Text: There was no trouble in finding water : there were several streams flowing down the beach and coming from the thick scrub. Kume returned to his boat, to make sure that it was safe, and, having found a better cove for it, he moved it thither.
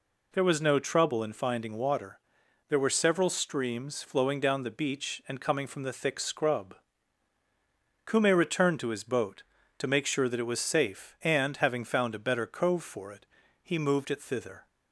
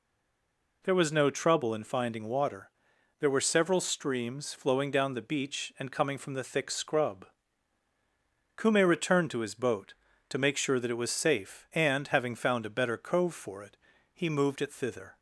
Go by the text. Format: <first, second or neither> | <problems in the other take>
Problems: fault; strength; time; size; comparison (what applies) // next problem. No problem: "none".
first | stays silent before the first word; slight; until 0.8 s; 0.8 s long